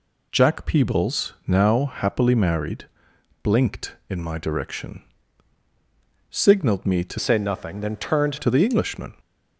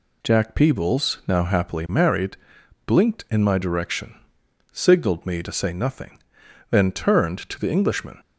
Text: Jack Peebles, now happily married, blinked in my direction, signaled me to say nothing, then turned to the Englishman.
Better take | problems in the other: second | changes voice from "say" to "turned"; from 7.1 to 8.3 s; 1.2 s long

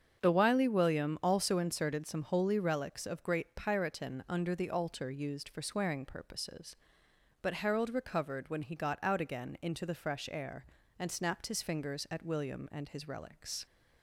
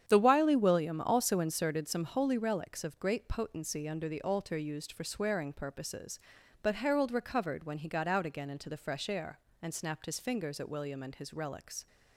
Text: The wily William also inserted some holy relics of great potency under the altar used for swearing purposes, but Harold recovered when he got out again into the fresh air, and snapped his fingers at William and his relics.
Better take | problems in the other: second | starts louder than the rest; strong; until 1.2 s; 7.5 dB; strong in the second // says "piratin" for "potency"; at 3.5 s

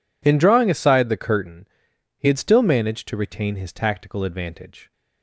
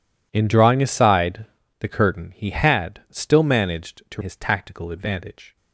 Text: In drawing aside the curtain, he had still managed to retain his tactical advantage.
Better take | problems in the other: first | pauses between "aside" and "the"; slight; at 1.4 s; 0.34 s long // skips "retain"; at 4.2 s

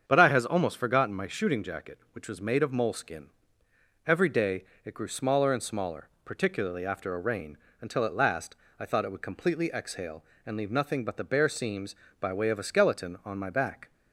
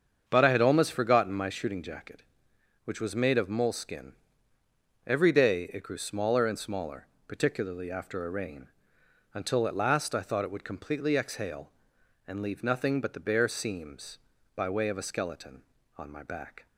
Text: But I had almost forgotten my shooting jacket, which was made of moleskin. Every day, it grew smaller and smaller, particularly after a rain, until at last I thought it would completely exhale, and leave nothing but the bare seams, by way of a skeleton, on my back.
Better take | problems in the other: second | starts louder than the rest; strong; until 1.0 s; 7.5 dB; strong in the second // says "has" for "had"; at 0.2 s // pauses between "last" and "I"; slight; at 8.5 s; 0.24 s long

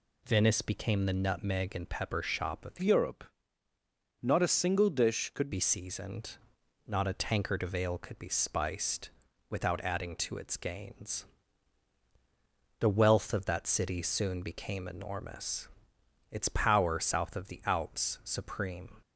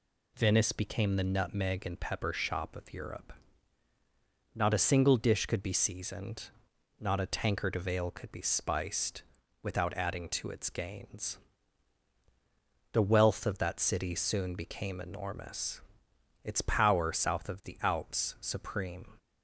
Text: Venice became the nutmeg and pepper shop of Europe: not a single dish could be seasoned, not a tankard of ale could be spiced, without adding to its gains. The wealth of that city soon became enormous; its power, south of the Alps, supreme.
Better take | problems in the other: second | changes voice from "Europe" to "could"; from 2.8 to 5.5 s; 2.7 s long

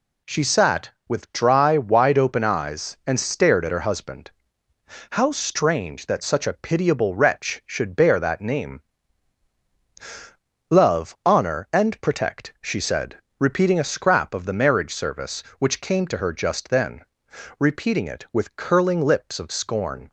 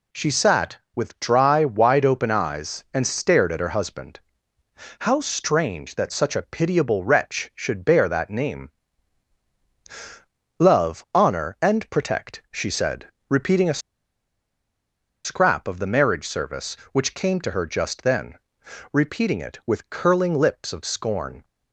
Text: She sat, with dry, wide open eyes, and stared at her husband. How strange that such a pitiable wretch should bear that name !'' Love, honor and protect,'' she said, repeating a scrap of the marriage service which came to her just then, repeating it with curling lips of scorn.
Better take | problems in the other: first | pauses between "a" and "scrap"; strong; at 13.8 s; 1.4 s long

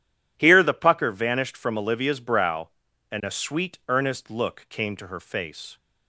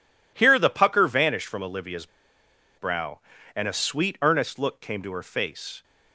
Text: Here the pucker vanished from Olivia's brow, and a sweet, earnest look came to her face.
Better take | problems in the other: first | pauses between "Olivia's" and "brow"; noticeable; at 2.0 s; 0.71 s long

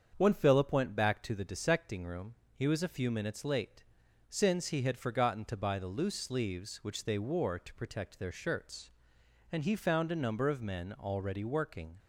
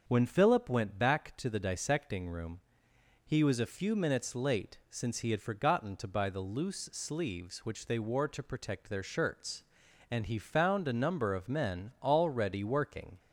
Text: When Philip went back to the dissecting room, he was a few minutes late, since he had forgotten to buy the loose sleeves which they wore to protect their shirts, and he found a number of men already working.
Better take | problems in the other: neither | starts louder than the rest; the same in both

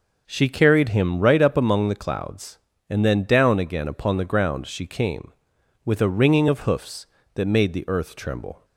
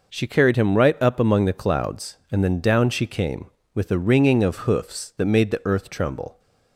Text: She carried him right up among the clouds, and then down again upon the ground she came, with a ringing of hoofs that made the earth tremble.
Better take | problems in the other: first | skips "again upon the ground"; at 2.8 s

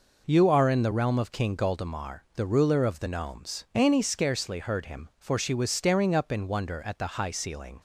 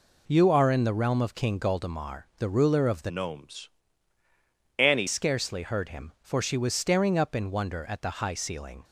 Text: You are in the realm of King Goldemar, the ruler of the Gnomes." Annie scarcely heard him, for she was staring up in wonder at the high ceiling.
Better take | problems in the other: first | changes voice from "Gnomes" to "Annie"; from 3.0 to 5.0 s; 2.0 s long

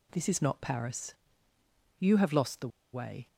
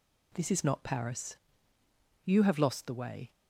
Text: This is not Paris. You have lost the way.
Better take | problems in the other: second | pauses between "the" and "way"; slight; at 2.6 s; 0.24 s long

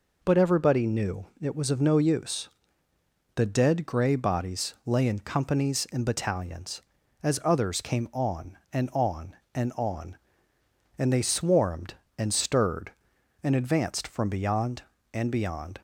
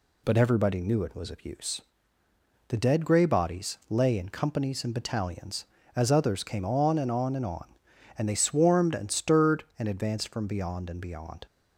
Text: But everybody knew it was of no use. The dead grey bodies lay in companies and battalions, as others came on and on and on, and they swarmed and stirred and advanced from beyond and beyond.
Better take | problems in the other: first | skips "no"; at 1.4 s

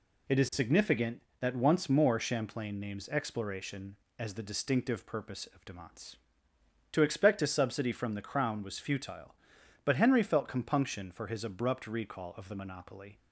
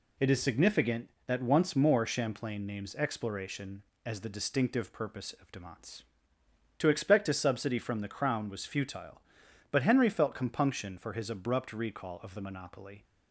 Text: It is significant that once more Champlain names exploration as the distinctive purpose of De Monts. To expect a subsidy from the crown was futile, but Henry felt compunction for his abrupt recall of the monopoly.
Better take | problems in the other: neither | none

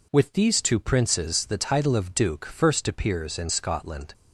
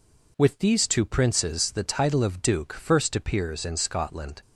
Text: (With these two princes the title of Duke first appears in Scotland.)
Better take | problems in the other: neither | none

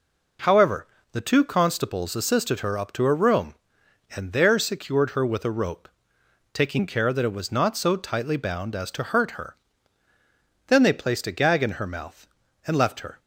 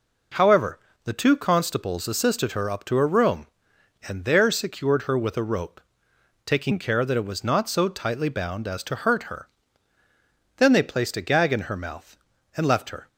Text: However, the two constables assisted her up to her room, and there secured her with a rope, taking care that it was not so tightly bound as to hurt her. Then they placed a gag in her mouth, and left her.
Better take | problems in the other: neither | none

